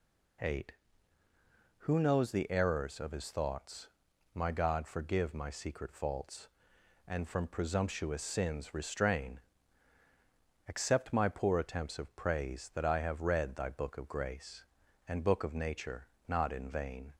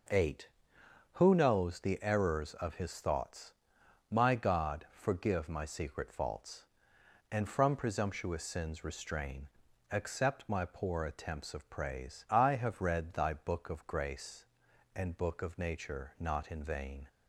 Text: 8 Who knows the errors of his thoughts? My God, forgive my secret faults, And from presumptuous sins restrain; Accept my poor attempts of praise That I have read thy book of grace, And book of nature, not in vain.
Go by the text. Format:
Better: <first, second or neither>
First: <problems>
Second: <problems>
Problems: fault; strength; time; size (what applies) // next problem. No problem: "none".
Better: first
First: none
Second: skips "That"; at 12.2 s